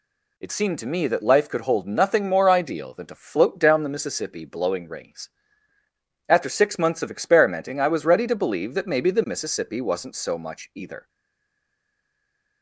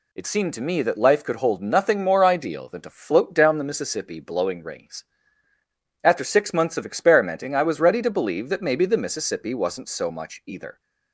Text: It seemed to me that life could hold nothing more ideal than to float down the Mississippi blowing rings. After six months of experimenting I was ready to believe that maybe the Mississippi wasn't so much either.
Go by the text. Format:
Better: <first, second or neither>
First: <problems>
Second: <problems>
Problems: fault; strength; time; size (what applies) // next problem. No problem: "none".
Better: second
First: stays silent after the last word; noticeable; from 11.0 s on; 1.6 s long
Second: none